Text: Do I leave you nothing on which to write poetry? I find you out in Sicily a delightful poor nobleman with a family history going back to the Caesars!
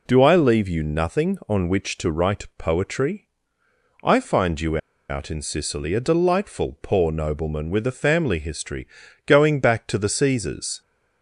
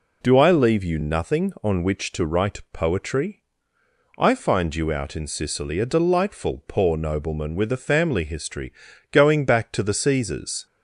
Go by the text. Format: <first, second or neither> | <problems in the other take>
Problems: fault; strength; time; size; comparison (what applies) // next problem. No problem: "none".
second | pauses between "you" and "out"; slight; at 4.7 s; 0.31 s long // pauses between "history" and "going"; at 8.8 s; 0.42 s long; also in the second